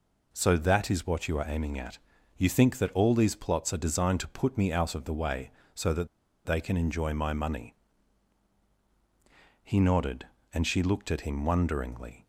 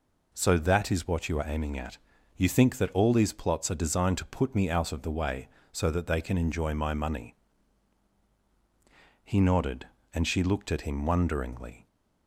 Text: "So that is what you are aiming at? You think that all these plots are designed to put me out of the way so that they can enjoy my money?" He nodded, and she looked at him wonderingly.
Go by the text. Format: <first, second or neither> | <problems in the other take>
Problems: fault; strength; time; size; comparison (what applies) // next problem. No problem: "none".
second | pauses between "that" and "they"; at 6.0 s; 0.38 s long